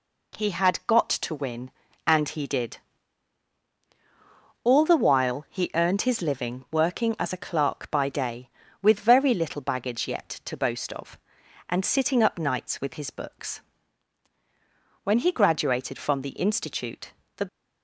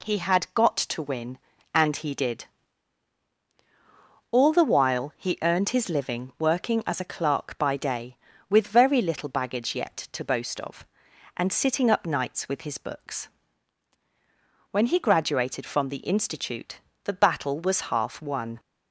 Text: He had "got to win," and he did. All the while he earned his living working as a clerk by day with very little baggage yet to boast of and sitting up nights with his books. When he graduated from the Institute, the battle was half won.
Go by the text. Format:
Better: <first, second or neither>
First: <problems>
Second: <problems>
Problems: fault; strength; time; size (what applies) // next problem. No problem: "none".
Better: second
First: stops before "battle was half won"; at 17.4 s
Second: none